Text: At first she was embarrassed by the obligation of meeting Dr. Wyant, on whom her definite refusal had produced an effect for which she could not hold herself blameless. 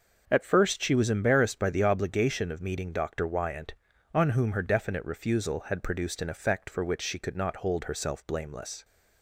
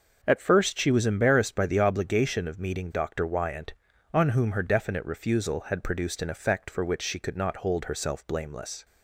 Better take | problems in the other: neither | starts louder than the rest; the same in both

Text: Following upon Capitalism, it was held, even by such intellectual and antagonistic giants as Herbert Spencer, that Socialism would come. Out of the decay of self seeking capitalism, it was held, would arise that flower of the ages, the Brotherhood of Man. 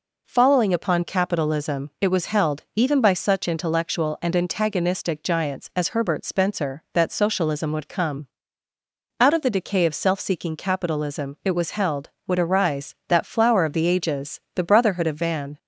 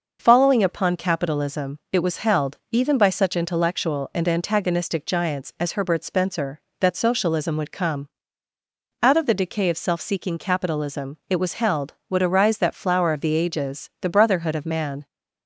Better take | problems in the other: second | says "Van" for "Man"; at 15.1 s

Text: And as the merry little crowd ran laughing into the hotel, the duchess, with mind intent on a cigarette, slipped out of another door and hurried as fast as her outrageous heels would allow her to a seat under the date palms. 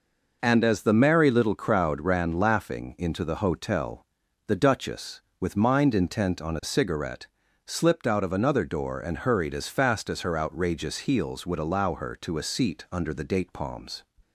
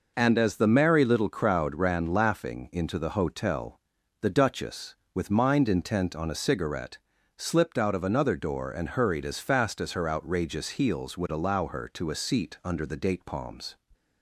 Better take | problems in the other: neither | none

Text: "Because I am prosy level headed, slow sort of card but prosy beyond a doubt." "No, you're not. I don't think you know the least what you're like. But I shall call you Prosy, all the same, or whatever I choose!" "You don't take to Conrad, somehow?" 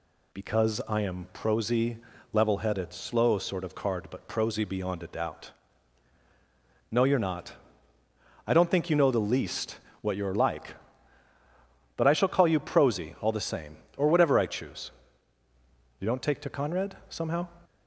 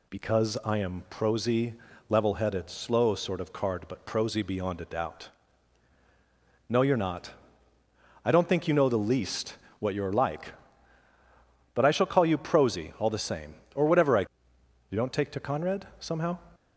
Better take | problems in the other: first | pauses between "prosy" and "level"; slight; at 1.7 s; 0.34 s long; slight in the first // pauses between "least" and "what"; slight; at 9.5 s; 0.22 s long; slight in the first // skips "choose"; at 14.5 s

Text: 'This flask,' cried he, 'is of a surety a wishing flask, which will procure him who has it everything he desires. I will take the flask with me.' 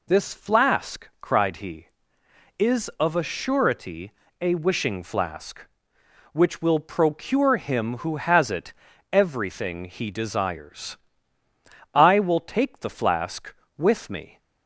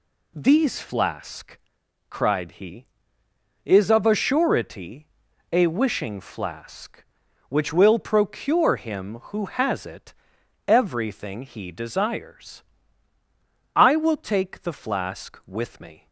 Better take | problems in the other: first | says "These" for "This"; at 0.3 s // pauses between "surety" and "a"; noticeable; at 5.0 s; 0.46 s long; slight in the first // pauses between "it" and "everything"; noticeable; at 10.1 s; 0.52 s long; also in the first

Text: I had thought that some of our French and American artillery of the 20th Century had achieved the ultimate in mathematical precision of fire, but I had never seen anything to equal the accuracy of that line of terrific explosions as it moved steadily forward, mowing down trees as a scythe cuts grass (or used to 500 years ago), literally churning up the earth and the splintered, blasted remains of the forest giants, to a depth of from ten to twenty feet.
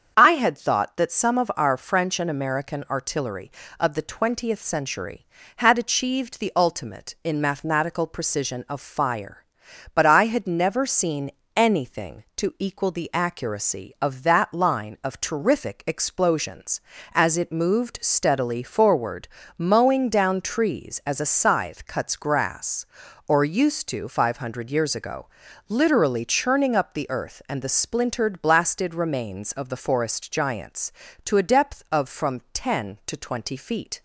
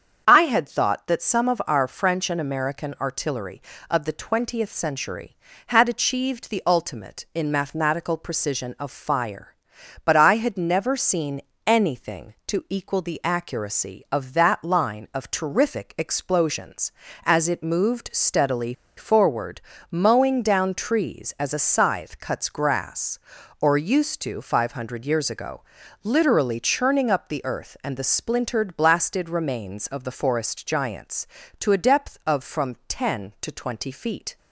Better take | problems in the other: first | starts louder than the rest; strong; until 1.2 s; 7 dB; strong in the first // pauses between "seen" and "anything"; slight; at 11.4 s; 0.26 s long; slight in the first // pauses between "steadily" and "forward"; slight; at 18.7 s; 0.24 s long

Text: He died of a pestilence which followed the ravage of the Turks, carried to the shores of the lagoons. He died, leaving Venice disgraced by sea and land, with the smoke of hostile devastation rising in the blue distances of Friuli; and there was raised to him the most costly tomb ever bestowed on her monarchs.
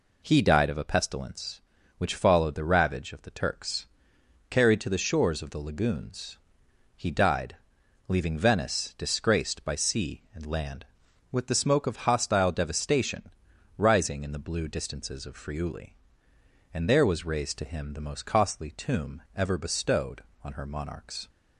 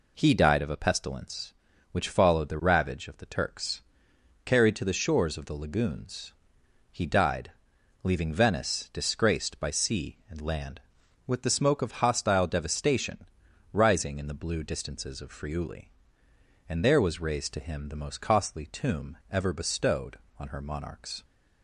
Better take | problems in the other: neither | pauses between "devastation" and "rising"; noticeable; the same in both

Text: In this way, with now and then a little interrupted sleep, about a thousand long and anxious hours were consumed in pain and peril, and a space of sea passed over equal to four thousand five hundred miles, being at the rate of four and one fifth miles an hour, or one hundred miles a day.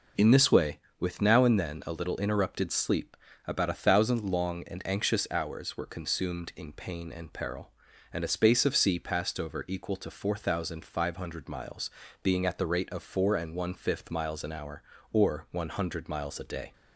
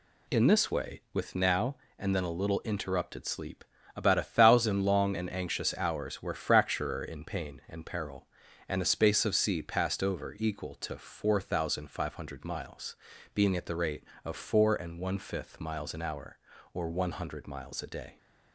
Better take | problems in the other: first | says "fracturer" for "consumed"; at 6.3 s

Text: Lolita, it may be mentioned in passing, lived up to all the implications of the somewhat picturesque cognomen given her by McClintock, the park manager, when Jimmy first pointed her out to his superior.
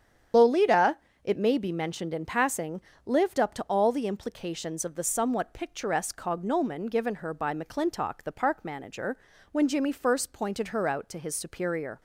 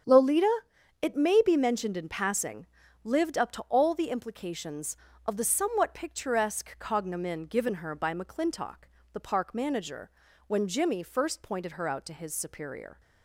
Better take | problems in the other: second | loses the start of "Lolita"; at 0.3 s; 80 ms // starts louder than the rest; strong; until 1.6 s; 8.5 dB; strong in the second

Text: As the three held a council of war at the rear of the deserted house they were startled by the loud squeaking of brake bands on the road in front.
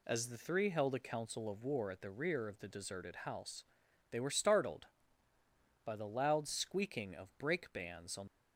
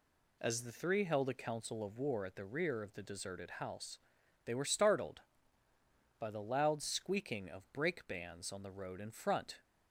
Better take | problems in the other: second | pauses between "house" and "they"; noticeable; at 3.6 s; 0.46 s long; noticeable in the second // stops before "the road in front"; at 8.2 s

